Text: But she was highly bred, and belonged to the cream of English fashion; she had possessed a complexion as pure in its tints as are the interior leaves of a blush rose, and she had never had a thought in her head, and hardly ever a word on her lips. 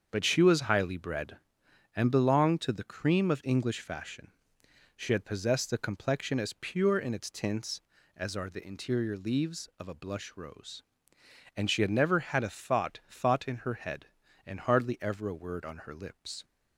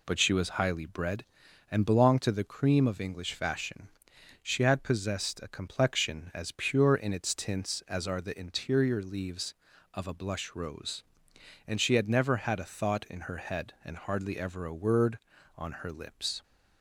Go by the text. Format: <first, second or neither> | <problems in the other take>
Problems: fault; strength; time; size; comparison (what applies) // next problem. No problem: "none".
second | starts louder than the rest; until 1.1 s; 7 dB // says "thought" twice; at 13.0 s